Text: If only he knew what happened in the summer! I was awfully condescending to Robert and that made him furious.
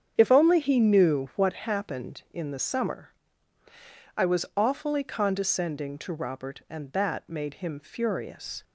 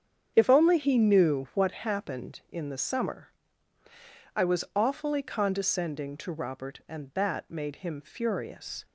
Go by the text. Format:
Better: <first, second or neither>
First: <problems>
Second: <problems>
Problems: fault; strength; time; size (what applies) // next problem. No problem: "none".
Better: neither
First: starts louder than the rest; strong; until 1.1 s; 8.5 dB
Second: starts louder than the rest; strong; until 1.3 s; 8.5 dB